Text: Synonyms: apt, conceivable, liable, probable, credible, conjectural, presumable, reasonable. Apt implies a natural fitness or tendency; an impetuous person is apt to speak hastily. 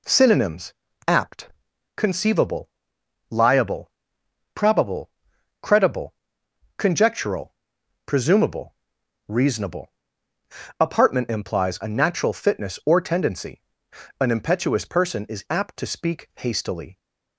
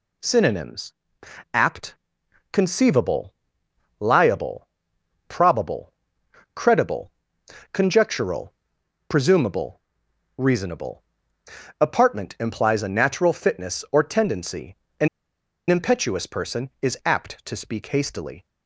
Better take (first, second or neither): first